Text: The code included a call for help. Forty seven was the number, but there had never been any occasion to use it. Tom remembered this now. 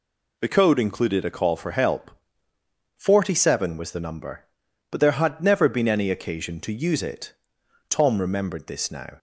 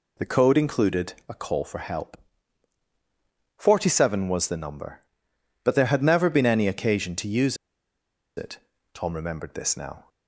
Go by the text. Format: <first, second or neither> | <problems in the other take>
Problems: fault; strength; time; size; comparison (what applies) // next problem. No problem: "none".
first | pauses between "use" and "it"; noticeable; at 7.5 s; 0.81 s long